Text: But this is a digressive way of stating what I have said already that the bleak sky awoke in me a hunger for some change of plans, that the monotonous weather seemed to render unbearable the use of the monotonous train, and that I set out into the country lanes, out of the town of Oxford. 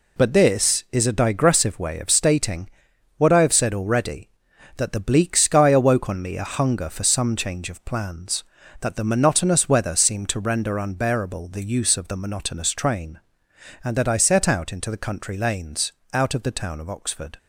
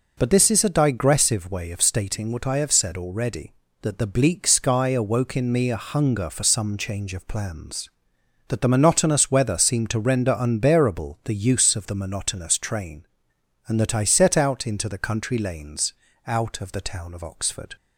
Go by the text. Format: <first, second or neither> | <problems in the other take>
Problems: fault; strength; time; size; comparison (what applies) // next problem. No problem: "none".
second | pauses between "stating" and "what"; noticeable; at 2.6 s; 0.48 s long // says "on" for "in"; at 6.0 s